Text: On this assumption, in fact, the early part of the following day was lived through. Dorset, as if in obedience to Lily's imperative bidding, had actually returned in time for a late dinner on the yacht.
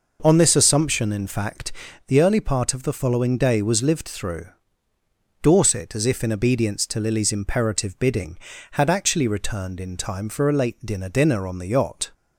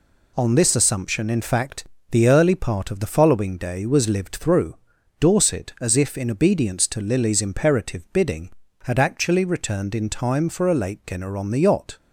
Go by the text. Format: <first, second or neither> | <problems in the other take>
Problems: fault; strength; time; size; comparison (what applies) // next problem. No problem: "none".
second | says "dinner" twice; at 11.0 s